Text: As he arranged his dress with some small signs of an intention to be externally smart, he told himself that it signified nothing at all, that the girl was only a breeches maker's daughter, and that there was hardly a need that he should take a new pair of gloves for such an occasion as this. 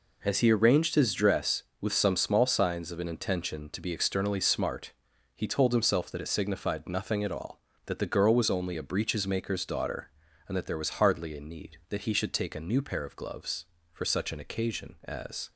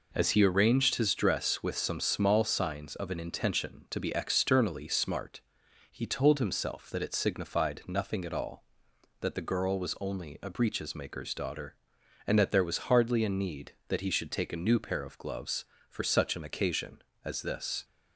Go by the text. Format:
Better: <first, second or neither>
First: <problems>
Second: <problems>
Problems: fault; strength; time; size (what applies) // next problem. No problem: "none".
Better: second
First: stops before "this"; at 15.5 s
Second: none